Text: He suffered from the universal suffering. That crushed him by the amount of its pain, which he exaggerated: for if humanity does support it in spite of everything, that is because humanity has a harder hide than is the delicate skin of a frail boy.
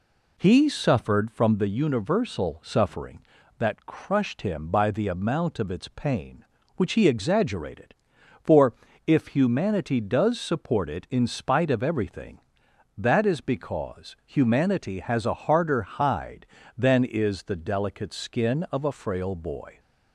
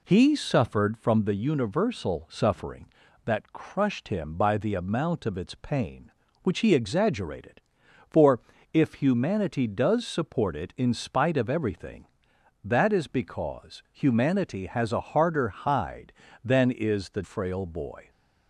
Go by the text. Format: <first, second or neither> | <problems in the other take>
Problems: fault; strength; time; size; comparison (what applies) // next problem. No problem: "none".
first | pauses between "for" and "if"; slight; at 8.4 s; 0.34 s long; slight in the first // skips "delicate skin of a"; at 17.2 s